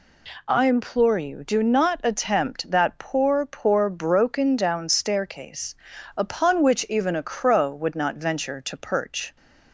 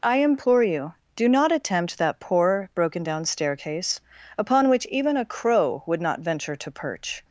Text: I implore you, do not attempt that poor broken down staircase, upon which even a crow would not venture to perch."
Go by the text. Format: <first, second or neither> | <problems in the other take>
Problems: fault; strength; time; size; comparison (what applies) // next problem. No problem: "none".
second | says "poor" twice; at 3.4 s